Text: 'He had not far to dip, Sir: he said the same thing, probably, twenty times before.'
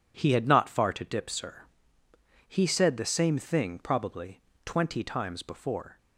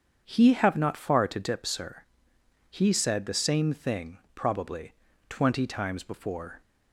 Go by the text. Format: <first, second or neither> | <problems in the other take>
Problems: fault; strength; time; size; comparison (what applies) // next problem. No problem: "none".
first | starts louder than the rest; strong; until 1.2 s; 7.5 dB // says "have" for "had"; at 0.5 s